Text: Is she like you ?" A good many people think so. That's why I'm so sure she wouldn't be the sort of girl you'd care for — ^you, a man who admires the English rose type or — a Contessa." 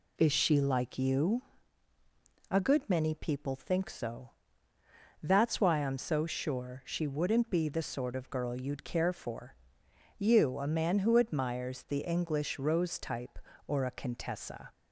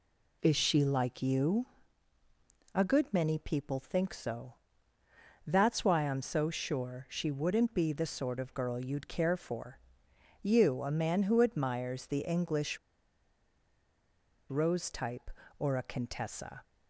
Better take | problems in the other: first | pauses between "English" and "rose"; strong; at 12.7 s; 1.7 s long

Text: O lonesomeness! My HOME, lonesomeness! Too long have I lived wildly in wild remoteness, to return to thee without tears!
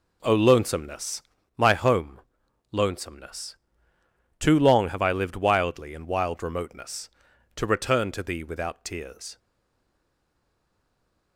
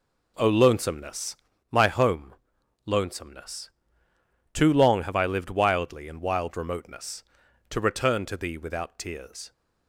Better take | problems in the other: second | stays silent after the last word; noticeable; from 9.3 s on; 2.0 s long

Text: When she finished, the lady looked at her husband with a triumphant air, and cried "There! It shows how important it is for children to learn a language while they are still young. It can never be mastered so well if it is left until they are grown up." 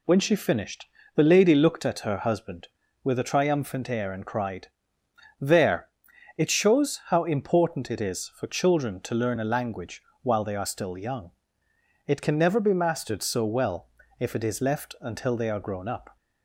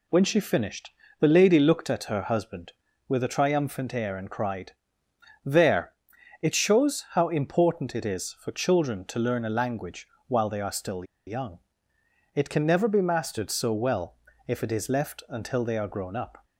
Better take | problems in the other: first | pauses between "cried" and "There"; noticeable; at 4.7 s; 0.72 s long; noticeable in the first // pauses between "language" and "while"; slight; at 10.0 s; 0.22 s long; slight in the first // pauses between "still" and "young"; slight; at 11.0 s; 0.23 s long // pauses between "well" and "if"; slight; at 14.1 s; 0.30 s long; slight in the first

